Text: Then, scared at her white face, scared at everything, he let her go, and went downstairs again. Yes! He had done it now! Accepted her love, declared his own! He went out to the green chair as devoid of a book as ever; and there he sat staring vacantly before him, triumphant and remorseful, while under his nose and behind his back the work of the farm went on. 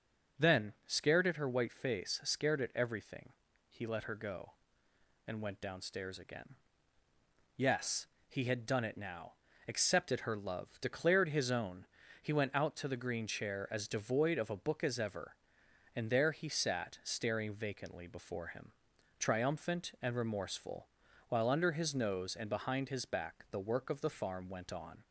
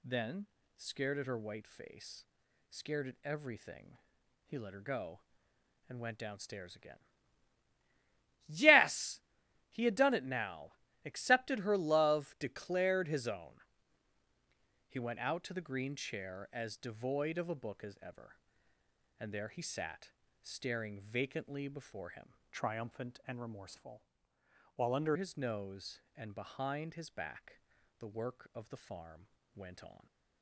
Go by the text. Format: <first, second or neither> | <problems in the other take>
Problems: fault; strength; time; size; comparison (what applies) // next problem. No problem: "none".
first | pauses between "sat" and "staring"; slight; at 20.0 s; 0.32 s long // changes voice from "triumphant" to "under"; from 22.5 to 25.1 s; 2.6 s long // pauses between "back" and "the"; at 27.5 s; 0.40 s long // pauses between "farm" and "went"; slight; at 29.2 s; 0.30 s long